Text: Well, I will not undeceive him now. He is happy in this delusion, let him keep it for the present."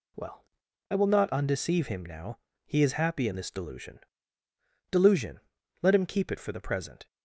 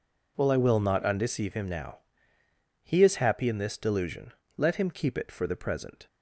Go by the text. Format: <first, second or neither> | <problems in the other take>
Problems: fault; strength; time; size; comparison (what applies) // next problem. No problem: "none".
second | says "delusion" twice; at 4.9 s